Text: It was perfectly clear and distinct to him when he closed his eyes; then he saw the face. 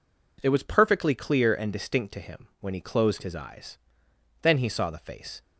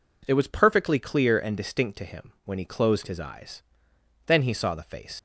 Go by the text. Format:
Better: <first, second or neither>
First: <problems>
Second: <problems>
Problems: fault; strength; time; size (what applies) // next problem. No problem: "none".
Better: first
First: none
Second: leaves "face" unfinished; at 5.1 s; 65 ms